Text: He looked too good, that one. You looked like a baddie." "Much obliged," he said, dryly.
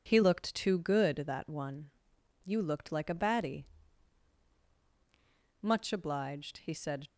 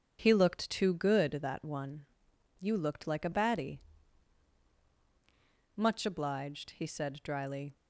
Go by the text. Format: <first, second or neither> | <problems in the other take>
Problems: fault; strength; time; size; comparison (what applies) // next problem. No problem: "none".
second | stops before "dryly"; at 7.0 s